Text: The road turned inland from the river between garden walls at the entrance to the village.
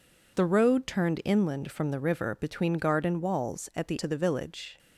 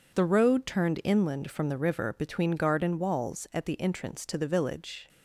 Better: second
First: skips "entrance"; at 3.9 s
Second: none

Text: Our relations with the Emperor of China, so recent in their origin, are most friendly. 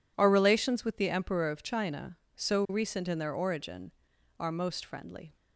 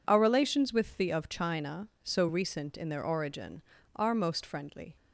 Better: first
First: none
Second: skips "Emperor"; at 1.1 s

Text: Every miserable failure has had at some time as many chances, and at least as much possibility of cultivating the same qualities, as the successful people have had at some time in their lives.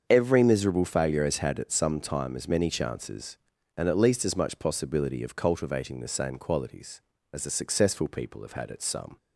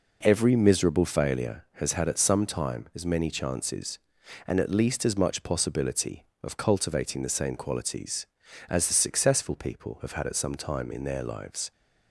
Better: second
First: starts louder than the rest; until 1.1 s; 7 dB // stops before "time in their lives"; at 9.1 s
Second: none

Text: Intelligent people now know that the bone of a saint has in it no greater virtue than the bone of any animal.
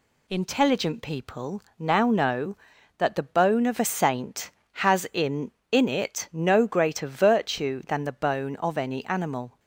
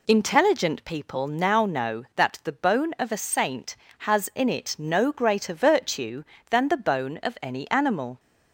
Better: second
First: pauses between "people" and "now"; slight; at 1.6 s; 0.16 s long // says "in" twice; at 5.7 s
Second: none

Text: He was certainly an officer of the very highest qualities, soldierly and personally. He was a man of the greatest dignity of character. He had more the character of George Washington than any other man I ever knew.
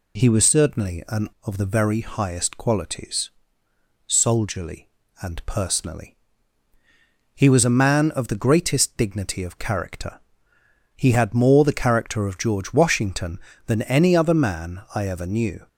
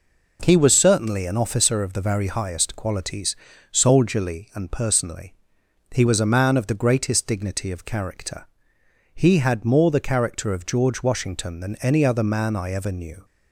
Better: second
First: skips "officer"; at 1.3 s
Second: none

